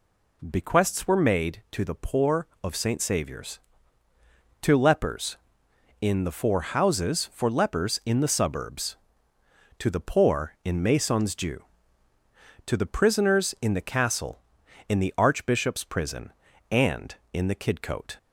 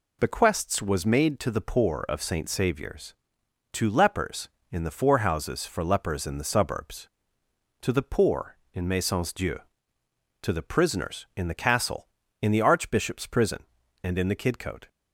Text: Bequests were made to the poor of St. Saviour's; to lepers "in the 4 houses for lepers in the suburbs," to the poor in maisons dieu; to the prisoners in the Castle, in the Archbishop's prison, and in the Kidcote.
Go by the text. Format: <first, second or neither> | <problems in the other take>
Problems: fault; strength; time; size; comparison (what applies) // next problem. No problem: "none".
first | says "was" for "were"; at 0.8 s